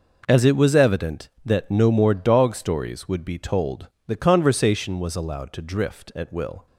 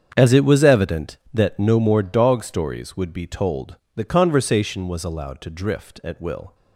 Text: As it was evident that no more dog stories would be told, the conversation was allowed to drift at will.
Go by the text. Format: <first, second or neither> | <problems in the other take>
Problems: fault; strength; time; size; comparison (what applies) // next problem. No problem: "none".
first | starts louder than the rest; strong; until 1.7 s; 8 dB